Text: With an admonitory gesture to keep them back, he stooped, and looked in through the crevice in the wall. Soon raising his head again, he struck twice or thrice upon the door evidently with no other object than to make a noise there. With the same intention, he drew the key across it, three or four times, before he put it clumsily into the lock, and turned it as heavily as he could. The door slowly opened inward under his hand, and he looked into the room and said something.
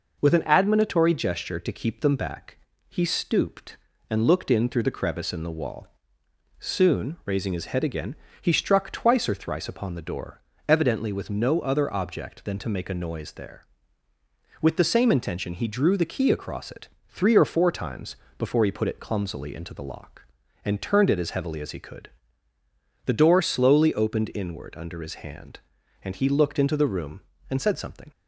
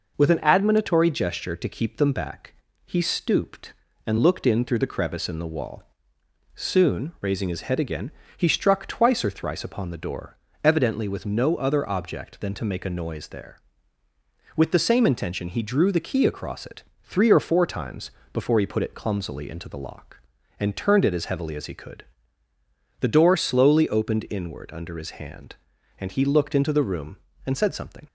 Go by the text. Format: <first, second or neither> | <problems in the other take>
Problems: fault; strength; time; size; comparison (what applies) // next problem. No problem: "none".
neither | pauses between "door" and "evidently"; slight; the same in both